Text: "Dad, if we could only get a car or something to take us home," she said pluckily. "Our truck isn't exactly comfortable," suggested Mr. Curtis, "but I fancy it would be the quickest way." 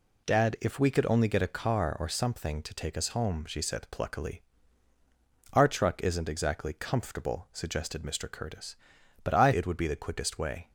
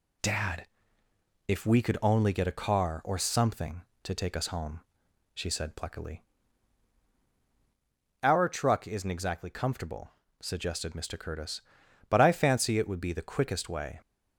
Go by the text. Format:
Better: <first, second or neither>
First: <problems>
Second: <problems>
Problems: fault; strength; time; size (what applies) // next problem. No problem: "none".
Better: second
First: skips "fancy"; at 9.5 s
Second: none